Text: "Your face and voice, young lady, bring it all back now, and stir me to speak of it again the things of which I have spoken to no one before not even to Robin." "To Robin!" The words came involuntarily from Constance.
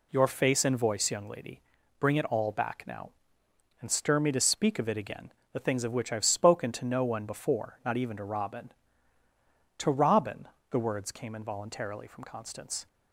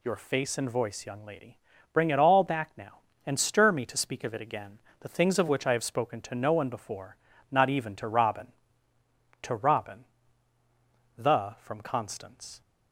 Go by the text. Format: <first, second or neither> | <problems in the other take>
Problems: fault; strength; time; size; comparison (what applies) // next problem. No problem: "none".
first | pauses between "again" and "the"; slight; at 4.7 s; 0.20 s long; slight in the first // pauses between "before" and "not"; slight; at 7.1 s; 0.34 s long // skips "words came involuntarily"; at 11.5 s